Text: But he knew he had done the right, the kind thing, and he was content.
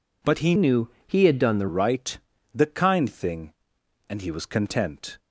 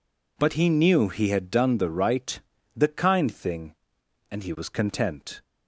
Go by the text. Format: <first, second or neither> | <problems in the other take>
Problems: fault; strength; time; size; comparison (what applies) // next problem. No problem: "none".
second | changes voice from "knew" to "the"; from 0.5 to 1.6 s; 1.1 s long // pauses between "knew" and "he"; slight; at 0.8 s; 0.16 s long